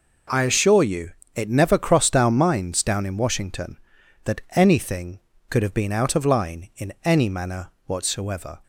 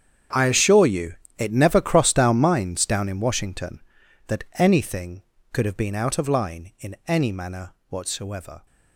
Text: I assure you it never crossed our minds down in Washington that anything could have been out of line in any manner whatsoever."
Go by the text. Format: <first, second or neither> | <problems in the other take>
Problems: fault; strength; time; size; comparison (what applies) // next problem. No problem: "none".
first | gets quieter; strong; throughout; 15.5 dB // pauses between "you" and "it"; slight; at 1.1 s; 0.22 s long; slight in the first // pauses between "manner" and "whatsoever"; slight; at 7.7 s; 0.16 s long; slight in the first